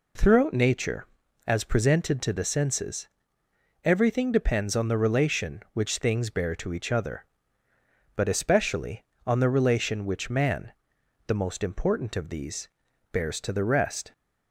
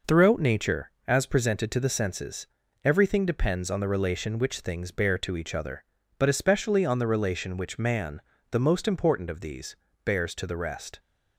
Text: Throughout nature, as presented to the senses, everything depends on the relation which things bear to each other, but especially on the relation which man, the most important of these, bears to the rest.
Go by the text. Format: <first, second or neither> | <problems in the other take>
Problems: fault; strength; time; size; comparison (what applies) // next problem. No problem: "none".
neither | none